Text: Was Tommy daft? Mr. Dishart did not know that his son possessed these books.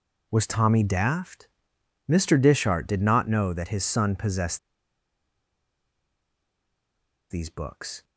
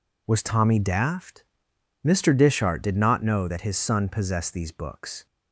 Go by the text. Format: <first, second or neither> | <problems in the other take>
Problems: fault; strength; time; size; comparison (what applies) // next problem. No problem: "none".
second | pauses between "possessed" and "these"; strong; at 4.5 s; 2.7 s long